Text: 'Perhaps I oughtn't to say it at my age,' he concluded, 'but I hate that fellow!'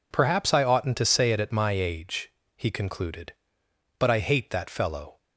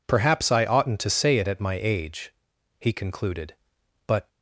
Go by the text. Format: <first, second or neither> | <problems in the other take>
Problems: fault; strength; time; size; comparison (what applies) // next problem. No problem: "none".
first | stops before "I hate that fellow"; at 4.2 s